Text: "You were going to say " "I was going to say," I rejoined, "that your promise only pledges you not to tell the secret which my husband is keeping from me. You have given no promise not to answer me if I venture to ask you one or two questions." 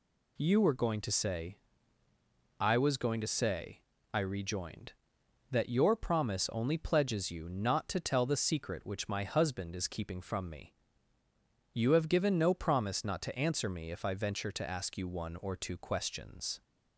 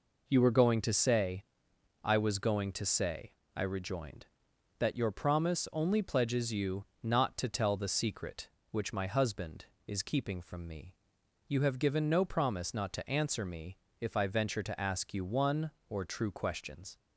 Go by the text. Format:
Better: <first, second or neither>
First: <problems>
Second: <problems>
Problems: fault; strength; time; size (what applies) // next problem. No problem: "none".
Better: first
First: none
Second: pauses between "you" and "not"; slight; at 6.8 s; 0.20 s long // pauses between "me" and "if"; slight; at 13.7 s; 0.22 s long // says "true" for "two"; at 16.0 s